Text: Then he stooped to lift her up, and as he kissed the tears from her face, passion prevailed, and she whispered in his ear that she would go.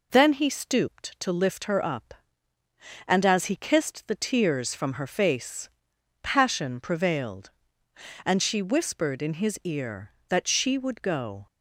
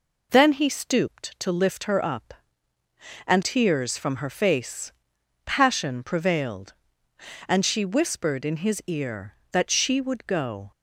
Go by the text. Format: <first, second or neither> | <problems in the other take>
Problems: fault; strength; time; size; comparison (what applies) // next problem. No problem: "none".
first | skips "as he kissed the"; at 3.4 s